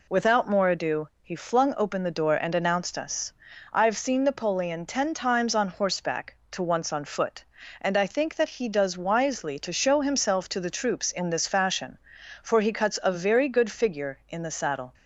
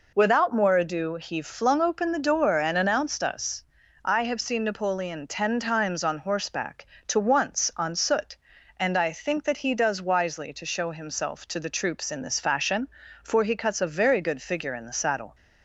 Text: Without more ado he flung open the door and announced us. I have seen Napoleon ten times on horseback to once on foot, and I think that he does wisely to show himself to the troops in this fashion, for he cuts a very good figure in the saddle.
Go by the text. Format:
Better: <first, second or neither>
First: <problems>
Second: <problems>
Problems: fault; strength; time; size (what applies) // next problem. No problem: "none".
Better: first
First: none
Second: says "soot" for "foot"; at 7.9 s